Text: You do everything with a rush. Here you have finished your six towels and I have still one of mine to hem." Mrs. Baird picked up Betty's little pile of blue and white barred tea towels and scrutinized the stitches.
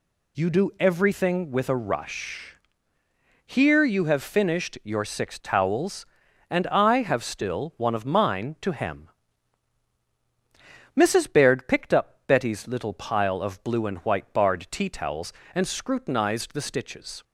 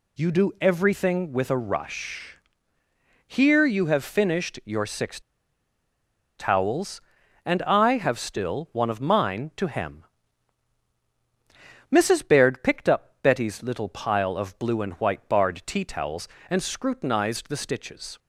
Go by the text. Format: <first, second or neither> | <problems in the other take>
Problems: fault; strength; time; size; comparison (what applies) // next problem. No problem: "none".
first | pauses between "six" and "towels"; at 5.2 s; 1.1 s long